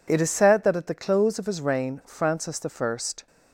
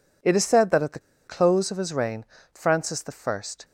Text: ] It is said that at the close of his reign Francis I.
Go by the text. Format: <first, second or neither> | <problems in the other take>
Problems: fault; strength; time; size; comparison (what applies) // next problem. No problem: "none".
first | pauses between "the" and "close"; slight; at 0.9 s; 0.28 s long // pauses between "reign" and "Francis"; slight; at 2.2 s; 0.28 s long